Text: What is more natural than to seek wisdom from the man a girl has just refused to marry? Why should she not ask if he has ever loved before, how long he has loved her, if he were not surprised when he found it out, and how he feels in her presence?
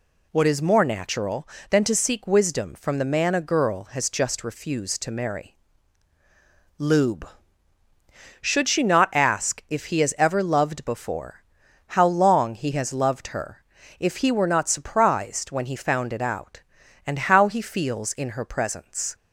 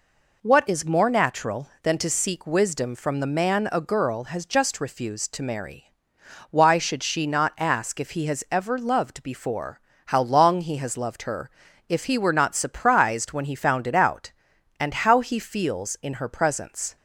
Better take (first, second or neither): second